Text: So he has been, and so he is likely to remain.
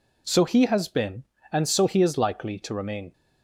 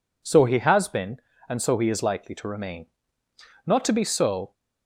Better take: first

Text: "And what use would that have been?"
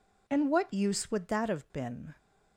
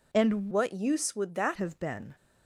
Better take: first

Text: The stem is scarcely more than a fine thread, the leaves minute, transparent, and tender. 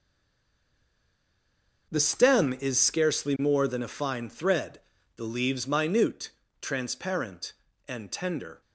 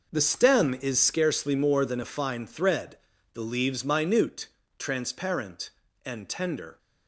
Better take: second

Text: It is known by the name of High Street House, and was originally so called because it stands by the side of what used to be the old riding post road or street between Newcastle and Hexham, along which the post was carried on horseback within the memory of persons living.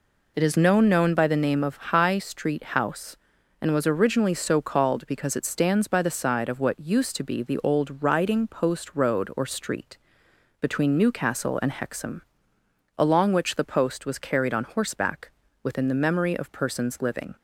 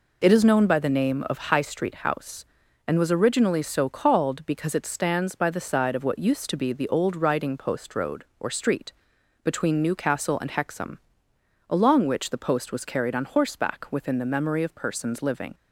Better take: second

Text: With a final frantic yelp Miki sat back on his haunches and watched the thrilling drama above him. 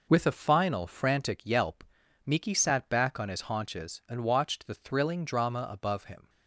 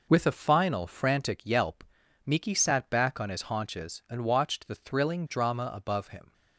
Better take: neither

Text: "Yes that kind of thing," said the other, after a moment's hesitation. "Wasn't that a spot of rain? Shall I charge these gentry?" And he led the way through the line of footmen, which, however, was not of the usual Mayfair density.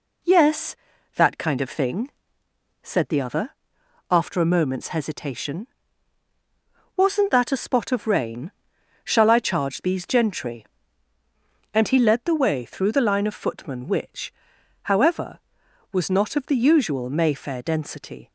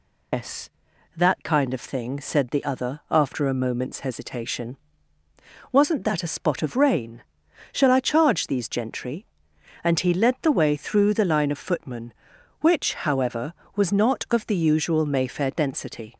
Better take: first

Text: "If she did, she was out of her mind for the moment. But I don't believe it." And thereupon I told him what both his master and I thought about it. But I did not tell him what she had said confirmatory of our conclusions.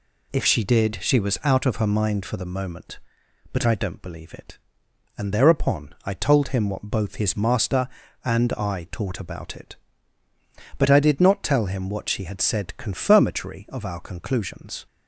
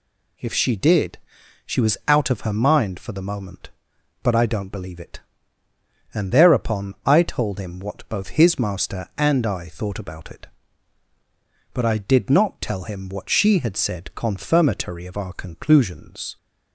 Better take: second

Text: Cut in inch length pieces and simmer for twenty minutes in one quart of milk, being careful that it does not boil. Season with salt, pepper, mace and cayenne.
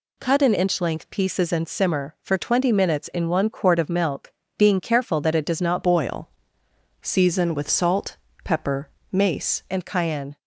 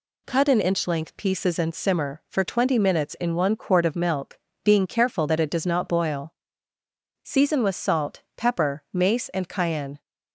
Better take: second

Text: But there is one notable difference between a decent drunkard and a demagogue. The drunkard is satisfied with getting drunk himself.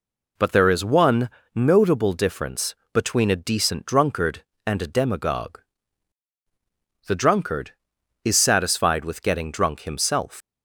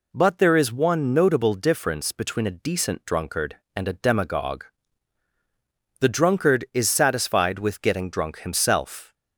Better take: second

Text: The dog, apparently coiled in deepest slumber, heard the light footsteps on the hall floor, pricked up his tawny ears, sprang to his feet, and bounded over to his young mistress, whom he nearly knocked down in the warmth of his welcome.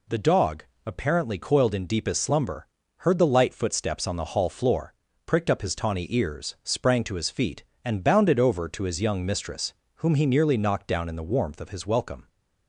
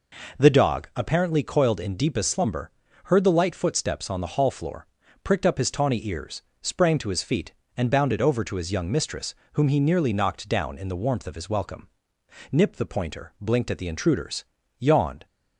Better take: first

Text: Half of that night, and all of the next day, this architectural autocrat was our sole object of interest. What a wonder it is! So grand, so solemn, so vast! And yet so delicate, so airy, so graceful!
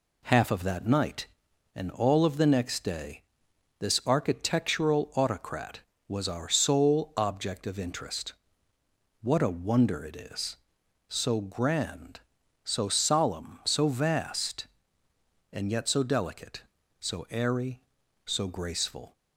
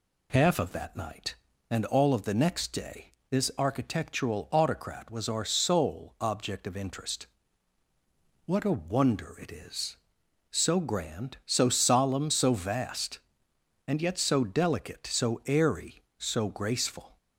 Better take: neither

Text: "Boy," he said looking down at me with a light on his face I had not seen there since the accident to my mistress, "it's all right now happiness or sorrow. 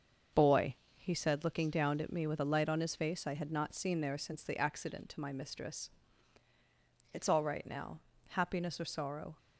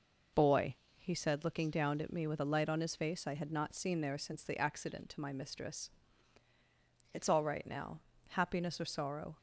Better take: second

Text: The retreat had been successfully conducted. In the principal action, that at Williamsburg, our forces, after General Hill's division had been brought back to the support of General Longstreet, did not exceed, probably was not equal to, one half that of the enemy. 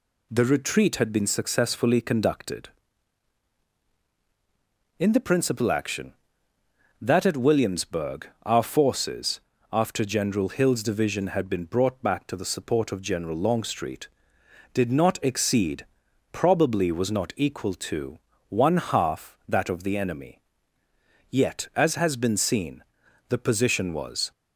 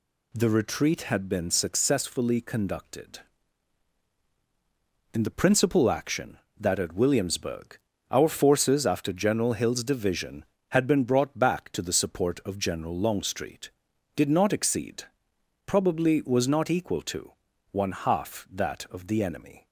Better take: second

